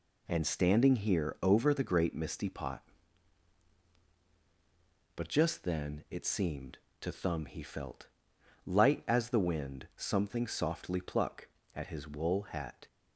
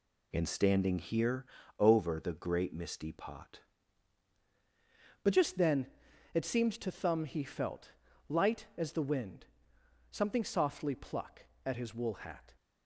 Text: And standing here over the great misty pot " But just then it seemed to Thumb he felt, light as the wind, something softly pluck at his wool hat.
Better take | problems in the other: first | pauses between "here" and "over"; slight; at 1.4 s; 0.34 s long // changes voice at "But"; from 5.2 s on; 7.3 s long // pauses between "then" and "it"; noticeable; at 5.8 s; 0.48 s long

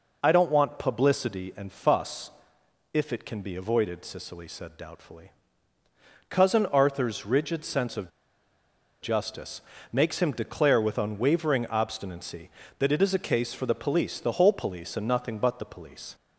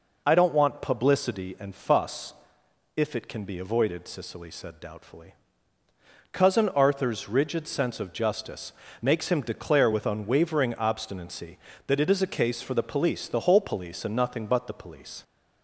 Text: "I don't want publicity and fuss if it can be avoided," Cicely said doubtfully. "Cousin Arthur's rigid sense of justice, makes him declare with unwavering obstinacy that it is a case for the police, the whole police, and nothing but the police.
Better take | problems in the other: second | pauses between "fuss" and "if"; noticeable; at 2.3 s; 0.62 s long; noticeable in the second // pauses between "of" and "justice"; noticeable; at 8.0 s; 0.93 s long

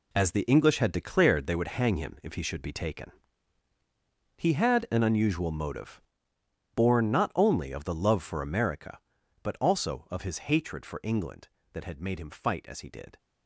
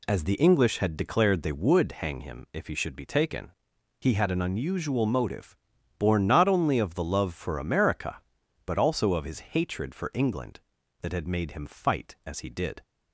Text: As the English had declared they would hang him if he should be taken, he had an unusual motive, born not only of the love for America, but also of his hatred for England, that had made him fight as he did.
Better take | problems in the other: second | gets quieter; strong; throughout; 9 dB

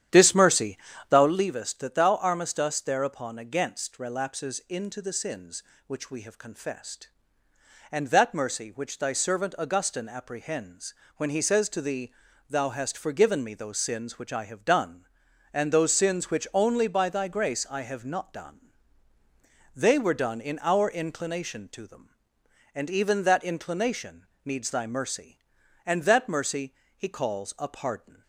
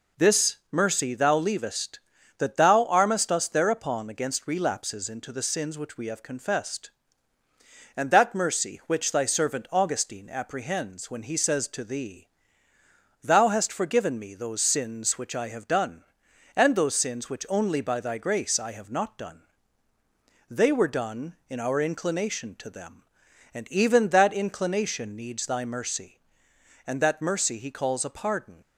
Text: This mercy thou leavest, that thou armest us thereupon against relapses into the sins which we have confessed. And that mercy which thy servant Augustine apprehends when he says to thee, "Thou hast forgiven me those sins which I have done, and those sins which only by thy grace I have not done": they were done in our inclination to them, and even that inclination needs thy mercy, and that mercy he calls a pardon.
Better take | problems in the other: second | starts louder than the rest; strong; until 1.5 s; 10 dB // pauses between "mercy" and "thou"; slight; at 0.7 s; 0.32 s long // pauses between "apprehends" and "when"; slight; at 10.9 s; 0.24 s long // pauses between "inclination" and "needs"; slight; at 24.2 s; 0.18 s long // pauses between "mercy" and "he"; slight; at 26.7 s; 0.22 s long

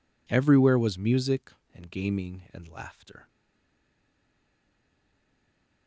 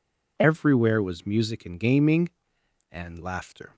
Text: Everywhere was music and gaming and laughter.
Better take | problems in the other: second | stays silent after the last word; strong; from 3.2 s on; 2.6 s long

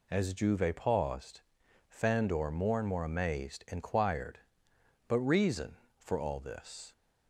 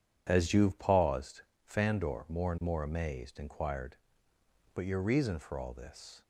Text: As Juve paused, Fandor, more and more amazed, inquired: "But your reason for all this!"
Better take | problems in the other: second | skips "your"; at 5.1 s

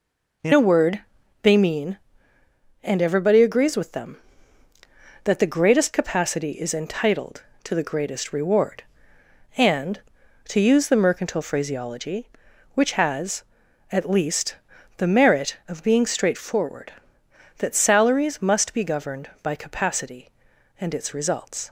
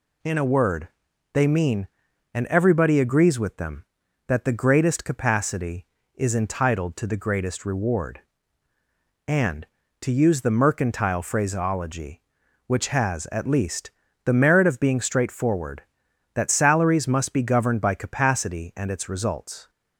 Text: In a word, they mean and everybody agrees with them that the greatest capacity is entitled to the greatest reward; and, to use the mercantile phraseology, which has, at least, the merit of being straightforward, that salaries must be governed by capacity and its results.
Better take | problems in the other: second | changes voice at "a"; from 0.5 s on; 21.1 s long

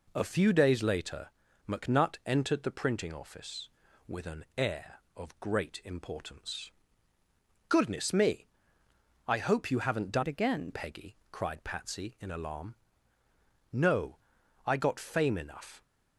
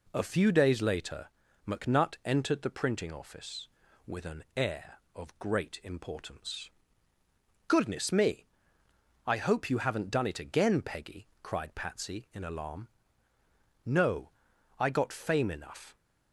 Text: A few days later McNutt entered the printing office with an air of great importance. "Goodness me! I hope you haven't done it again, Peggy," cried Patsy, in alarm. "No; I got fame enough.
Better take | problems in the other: second | pauses between "later" and "McNutt"; at 1.2 s; 0.40 s long; also in the second // changes voice from "it" to "again"; from 10.2 to 10.7 s; 0.5 s long

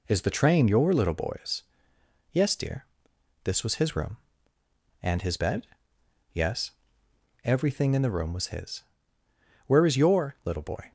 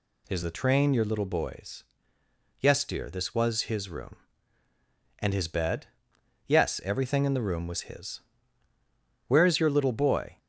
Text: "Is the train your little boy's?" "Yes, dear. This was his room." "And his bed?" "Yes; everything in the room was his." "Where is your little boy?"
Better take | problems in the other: neither | none

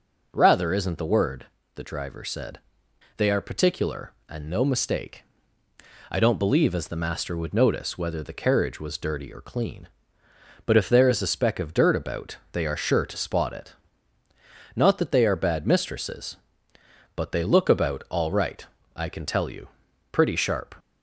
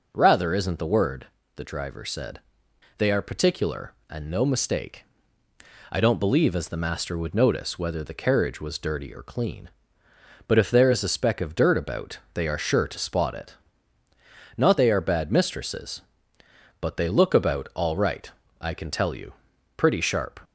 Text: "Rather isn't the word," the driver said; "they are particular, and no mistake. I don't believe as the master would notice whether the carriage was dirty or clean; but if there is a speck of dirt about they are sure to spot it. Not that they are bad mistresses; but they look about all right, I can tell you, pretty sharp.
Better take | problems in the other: first | pauses between "about" and "they"; slight; at 12.1 s; 0.16 s long; slight in the first // skips "that"; at 14.7 s

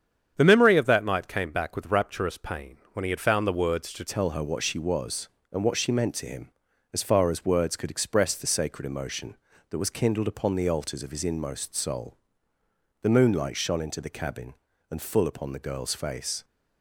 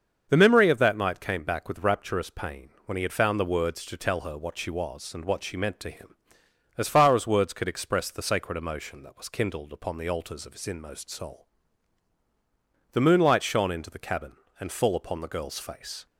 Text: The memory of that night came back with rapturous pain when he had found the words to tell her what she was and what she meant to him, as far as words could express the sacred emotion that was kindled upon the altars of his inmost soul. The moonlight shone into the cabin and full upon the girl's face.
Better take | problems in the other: second | starts louder than the rest; strong; until 1.3 s; 8 dB; also in the second // pauses between "pain" and "when"; slight; at 2.7 s; 0.16 s long; slight in the second // changes voice at "tell"; from 4.0 s on; 12.4 s long

